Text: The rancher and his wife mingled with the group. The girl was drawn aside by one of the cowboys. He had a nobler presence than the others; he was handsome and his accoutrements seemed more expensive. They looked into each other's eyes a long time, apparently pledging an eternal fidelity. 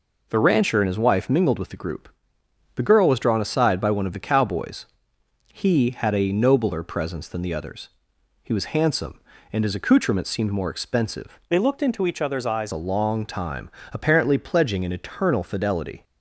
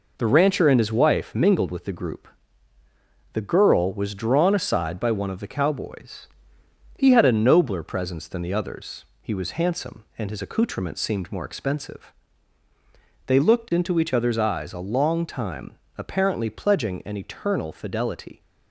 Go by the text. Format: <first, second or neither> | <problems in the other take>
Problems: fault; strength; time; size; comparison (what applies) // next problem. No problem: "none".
second | changes voice from "They" to "eyes"; from 11.4 to 12.7 s; 1.3 s long